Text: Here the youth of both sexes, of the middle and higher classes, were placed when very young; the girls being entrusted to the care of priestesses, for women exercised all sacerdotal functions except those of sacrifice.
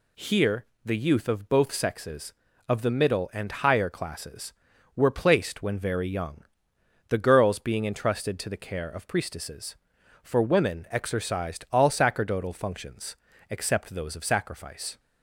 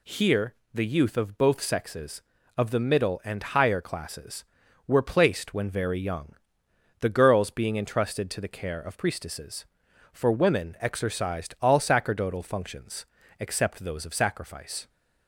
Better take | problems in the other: neither | pauses between "Here" and "the"; slight; the same in both // pauses between "functions" and "except"; slight; the same in both

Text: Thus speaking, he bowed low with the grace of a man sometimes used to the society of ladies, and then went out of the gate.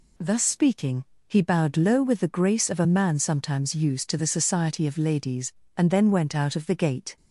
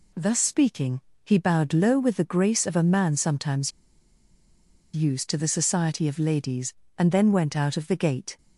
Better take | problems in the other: first | pauses between "sometimes" and "used"; at 3.7 s; 1.2 s long

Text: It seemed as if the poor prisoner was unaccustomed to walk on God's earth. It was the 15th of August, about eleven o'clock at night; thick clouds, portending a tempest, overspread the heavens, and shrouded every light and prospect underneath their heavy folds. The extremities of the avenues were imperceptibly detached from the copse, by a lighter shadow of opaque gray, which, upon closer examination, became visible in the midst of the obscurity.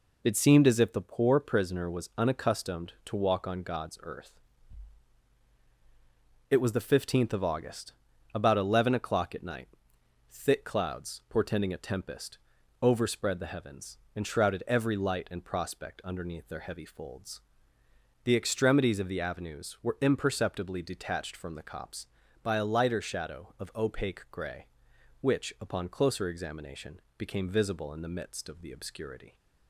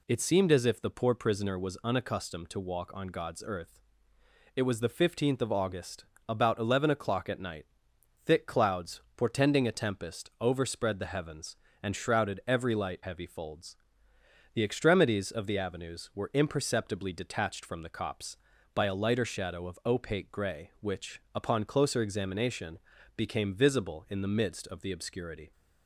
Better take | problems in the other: first | skips "and prospect underneath their"; at 13.0 s

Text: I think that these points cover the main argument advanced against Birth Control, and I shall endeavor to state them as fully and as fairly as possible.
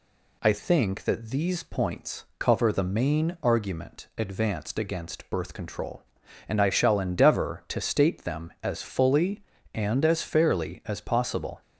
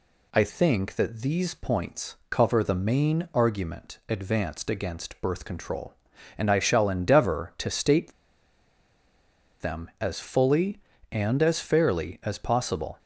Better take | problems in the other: first | pauses between "points" and "cover"; slight; at 2.1 s; 0.16 s long; slight in the first // pauses between "state" and "them"; strong; at 8.1 s; 1.4 s long

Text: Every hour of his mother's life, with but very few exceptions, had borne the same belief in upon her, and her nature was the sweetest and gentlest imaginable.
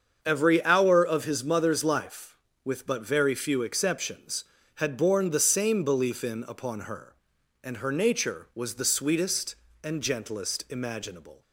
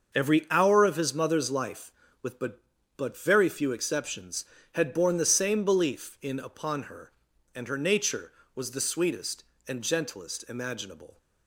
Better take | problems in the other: first | starts louder than the rest; until 1.2 s; 6 dB; also in the first // says "but" twice; at 2.9 s

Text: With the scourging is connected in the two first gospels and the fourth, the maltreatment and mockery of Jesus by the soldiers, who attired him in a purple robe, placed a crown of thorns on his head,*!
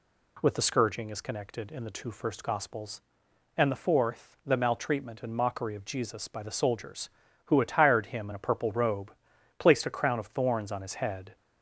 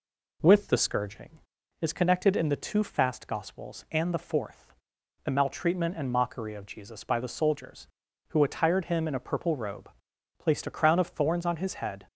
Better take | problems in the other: first | says "fast" for "first"; at 2.8 s

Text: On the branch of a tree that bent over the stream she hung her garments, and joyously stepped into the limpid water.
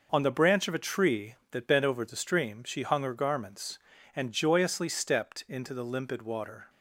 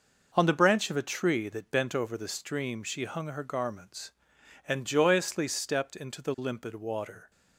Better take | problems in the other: neither | none

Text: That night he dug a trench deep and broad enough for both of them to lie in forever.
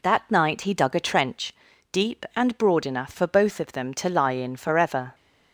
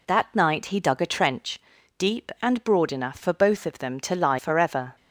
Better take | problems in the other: first | pauses between "trench" and "deep"; at 1.5 s; 0.40 s long; also in the first // skips "in"; at 4.3 s

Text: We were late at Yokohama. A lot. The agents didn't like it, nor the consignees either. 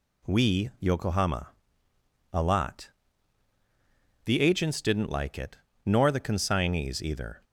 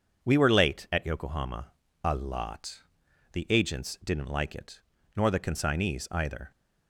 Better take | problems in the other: second | skips "were late at"; at 0.7 s

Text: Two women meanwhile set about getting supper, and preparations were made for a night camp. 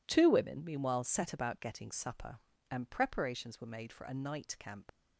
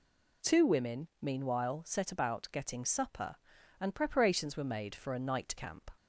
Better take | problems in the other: second | leaves "camp" unfinished; at 4.8 s; 40 ms

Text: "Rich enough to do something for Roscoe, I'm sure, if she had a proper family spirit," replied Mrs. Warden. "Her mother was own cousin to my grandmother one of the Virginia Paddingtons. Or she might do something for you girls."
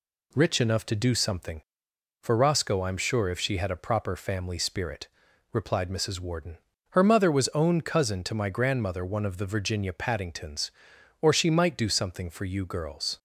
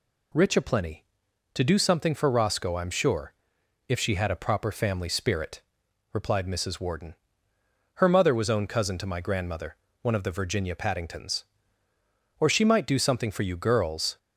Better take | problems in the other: first | says "aplenty" for "enough"; at 0.5 s // pauses between "grandmother" and "one"; slight; at 9.7 s; 0.26 s long

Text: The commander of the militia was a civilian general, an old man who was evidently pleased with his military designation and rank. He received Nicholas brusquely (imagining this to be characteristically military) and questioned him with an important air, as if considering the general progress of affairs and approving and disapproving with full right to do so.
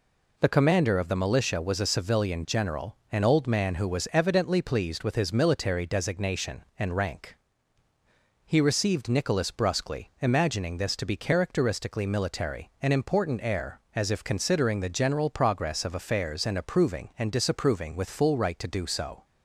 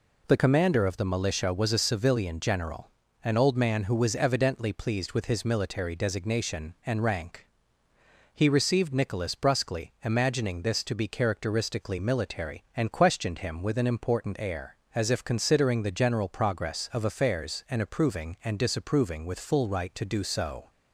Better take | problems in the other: second | skips "and questioned him with"; at 12.7 s

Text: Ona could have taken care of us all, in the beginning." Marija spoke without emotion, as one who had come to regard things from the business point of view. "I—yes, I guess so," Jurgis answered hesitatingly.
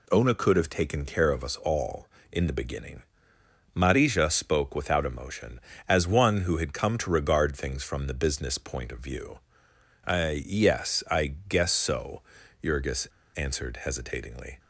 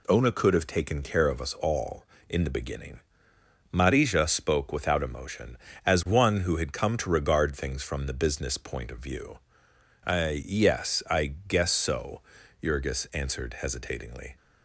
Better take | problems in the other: second | pauses between "Jurgis" and "answered"; slight; at 13.0 s; 0.30 s long

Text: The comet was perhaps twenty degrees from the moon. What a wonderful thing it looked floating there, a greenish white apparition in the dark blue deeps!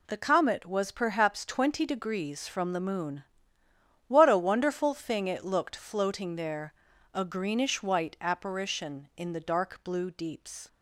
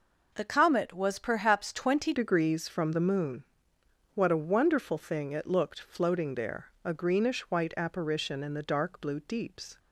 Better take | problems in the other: first | changes voice at "degrees"; from 2.1 s on; 7.6 s long

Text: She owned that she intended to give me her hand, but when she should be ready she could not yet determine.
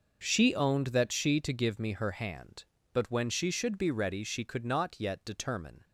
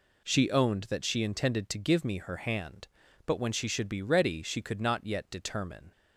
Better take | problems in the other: second | skips "intended"; at 1.3 s

